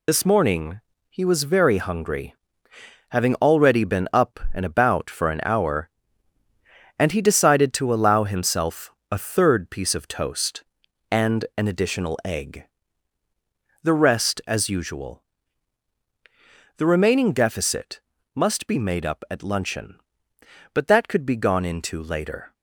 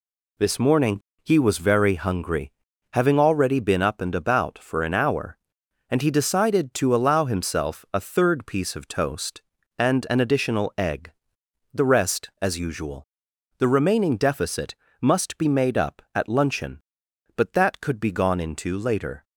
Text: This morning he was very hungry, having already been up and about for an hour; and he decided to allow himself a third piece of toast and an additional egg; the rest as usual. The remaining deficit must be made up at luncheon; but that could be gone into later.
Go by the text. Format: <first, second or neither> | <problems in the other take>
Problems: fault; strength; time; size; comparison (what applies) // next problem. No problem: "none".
second | loses the start of "This"; at 0.0 s; 45 ms // pauses between "morning" and "he"; slight; at 0.7 s; 0.30 s long; slight in the second // pauses between "himself" and "a"; slight; at 8.8 s; 0.22 s long // pauses between "deficit" and "must"; slight; at 17.9 s; 0.34 s long; slight in the second